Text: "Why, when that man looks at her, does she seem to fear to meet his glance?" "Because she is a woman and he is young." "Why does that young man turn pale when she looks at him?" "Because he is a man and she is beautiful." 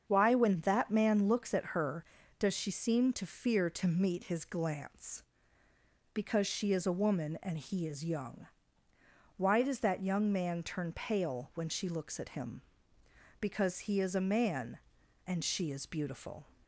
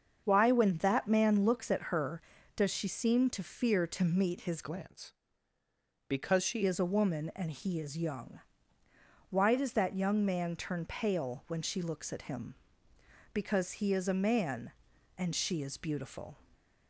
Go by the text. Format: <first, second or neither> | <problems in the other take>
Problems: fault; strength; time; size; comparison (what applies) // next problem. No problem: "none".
first | starts louder than the rest; until 1.2 s; 6.5 dB; also in the first // changes voice from "glance" to "she"; from 4.6 to 6.6 s; 2.0 s long